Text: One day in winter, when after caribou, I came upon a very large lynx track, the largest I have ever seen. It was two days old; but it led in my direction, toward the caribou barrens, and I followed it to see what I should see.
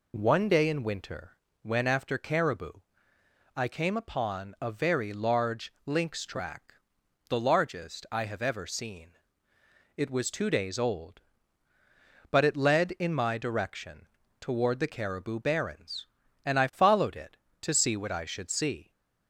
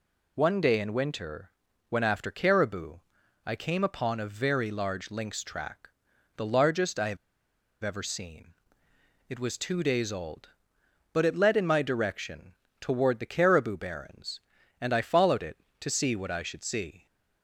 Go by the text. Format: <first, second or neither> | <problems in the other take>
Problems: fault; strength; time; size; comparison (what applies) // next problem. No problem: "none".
first | pauses between "have" and "ever"; noticeable; at 7.1 s; 0.66 s long